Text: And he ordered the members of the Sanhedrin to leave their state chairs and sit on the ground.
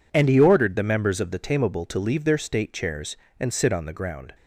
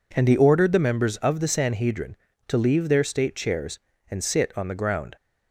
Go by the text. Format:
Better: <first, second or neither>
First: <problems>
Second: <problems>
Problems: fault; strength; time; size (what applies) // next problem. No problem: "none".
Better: second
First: says "Tameable" for "Sanhedrin"; at 1.3 s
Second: none